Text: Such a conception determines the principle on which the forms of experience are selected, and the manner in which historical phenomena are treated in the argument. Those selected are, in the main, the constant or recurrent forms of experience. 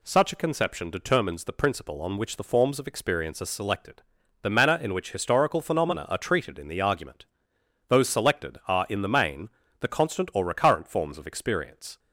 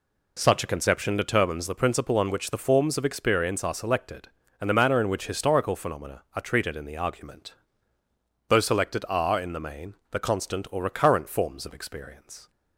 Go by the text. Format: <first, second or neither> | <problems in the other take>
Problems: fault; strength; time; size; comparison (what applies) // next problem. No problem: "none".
second | skips "and"; at 4.2 s